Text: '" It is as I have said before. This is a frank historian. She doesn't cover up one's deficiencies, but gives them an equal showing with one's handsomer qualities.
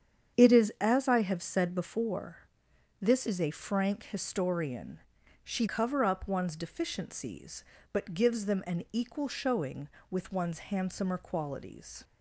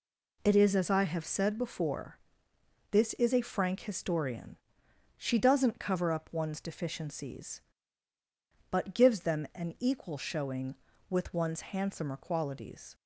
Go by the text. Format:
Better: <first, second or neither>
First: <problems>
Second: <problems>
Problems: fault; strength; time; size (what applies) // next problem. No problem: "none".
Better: second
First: starts louder than the rest; strong; until 1.4 s; 8 dB // skips "doesn't"; at 5.6 s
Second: none